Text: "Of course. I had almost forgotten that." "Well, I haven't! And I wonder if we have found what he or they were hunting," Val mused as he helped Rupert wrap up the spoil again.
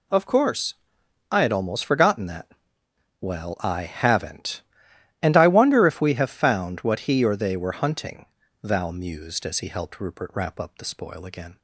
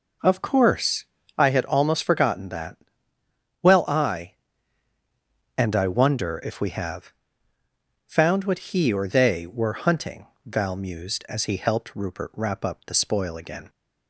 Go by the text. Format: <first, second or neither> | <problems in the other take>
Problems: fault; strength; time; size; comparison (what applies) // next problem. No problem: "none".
first | skips "haven't"; at 4.9 s // pauses between "have" and "found"; noticeable; at 7.1 s; 0.96 s long